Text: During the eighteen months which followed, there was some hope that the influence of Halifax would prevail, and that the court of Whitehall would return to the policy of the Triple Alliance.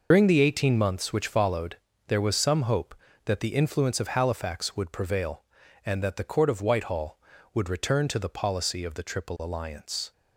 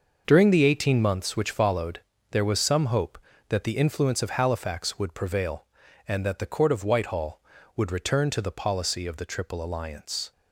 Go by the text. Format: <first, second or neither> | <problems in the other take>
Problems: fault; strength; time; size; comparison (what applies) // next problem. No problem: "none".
second | loses the start of "During"; at 0.1 s; 70 ms